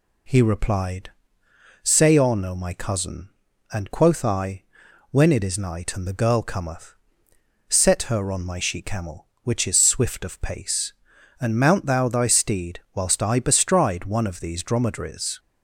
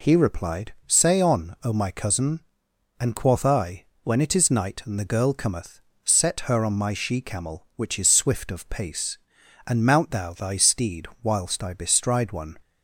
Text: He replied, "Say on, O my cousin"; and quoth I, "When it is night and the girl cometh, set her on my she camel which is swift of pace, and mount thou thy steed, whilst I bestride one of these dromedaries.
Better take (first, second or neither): first